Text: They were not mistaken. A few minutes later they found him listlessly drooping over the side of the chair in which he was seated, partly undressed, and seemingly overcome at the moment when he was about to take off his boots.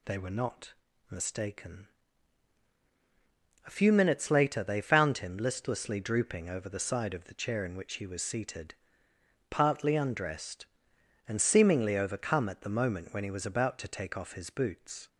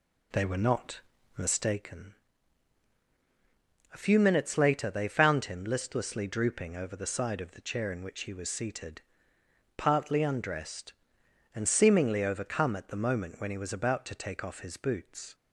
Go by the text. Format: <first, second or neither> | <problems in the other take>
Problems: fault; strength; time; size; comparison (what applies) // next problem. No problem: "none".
first | starts louder than the rest; slight; until 1.9 s; 2 dB // pauses between "not" and "mistaken"; slight; at 1.0 s; 0.36 s long; slight in the first